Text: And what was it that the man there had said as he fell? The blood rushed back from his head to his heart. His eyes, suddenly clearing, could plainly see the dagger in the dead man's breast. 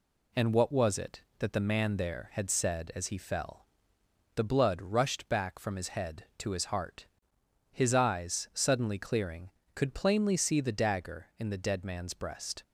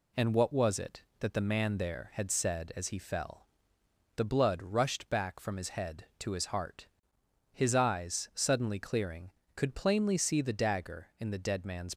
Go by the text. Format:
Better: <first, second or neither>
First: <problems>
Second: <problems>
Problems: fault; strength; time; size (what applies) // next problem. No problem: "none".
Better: first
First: none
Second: stops before "breast"; at 11.9 s